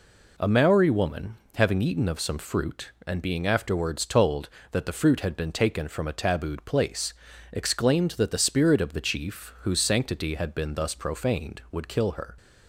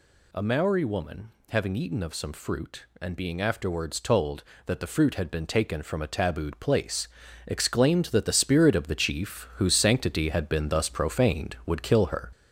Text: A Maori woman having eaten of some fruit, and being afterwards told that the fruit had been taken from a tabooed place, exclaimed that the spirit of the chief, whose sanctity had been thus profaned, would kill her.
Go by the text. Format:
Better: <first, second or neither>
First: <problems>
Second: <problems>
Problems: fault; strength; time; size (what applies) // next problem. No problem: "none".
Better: first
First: pauses between "woman" and "having"; slight; at 1.3 s; 0.18 s long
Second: gets louder; noticeable; throughout; 4.5 dB // pauses between "woman" and "having"; slight; at 1.3 s; 0.18 s long